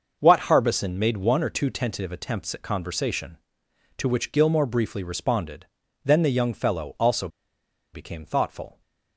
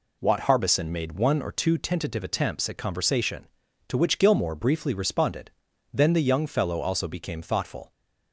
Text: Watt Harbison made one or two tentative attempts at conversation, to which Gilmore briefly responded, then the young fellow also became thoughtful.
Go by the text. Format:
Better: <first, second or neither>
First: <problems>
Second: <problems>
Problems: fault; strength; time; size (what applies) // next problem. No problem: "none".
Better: second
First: starts louder than the rest; noticeable; until 1.2 s; 6 dB // pauses between "also" and "became"; noticeable; at 7.2 s; 0.65 s long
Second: none